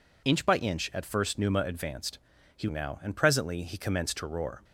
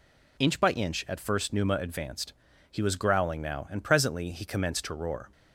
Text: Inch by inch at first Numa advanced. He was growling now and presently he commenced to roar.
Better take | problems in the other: second | skips "was growling"; at 2.6 s

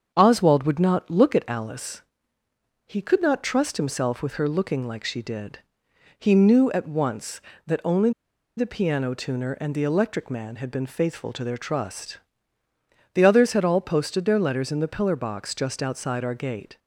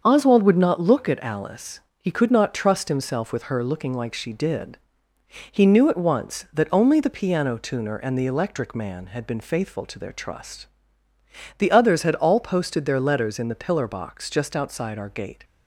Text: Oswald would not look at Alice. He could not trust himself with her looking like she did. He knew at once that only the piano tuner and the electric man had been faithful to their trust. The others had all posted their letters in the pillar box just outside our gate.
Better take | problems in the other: second | starts louder than the rest; until 1.1 s; 7 dB; also in the second // pauses between "only" and "the"; noticeable; at 8.1 s; 0.46 s long

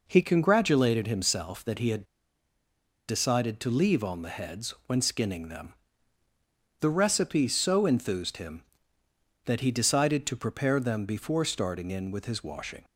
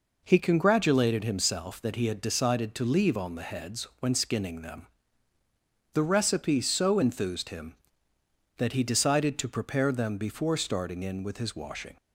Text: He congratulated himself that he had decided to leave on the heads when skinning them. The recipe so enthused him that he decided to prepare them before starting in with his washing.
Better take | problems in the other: second | pauses between "had" and "decided"; at 2.0 s; 1.0 s long

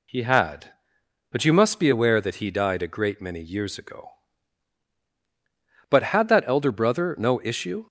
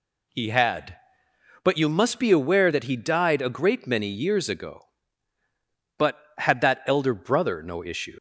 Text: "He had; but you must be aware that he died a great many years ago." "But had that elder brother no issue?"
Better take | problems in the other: first | leaves "issue" unfinished; at 8.1 s; 115 ms

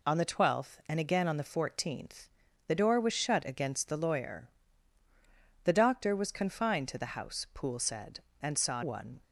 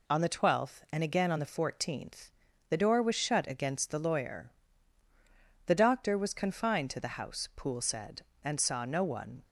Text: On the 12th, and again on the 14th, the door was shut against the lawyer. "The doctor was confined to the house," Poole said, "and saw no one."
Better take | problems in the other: second | skips "no"; at 8.8 s

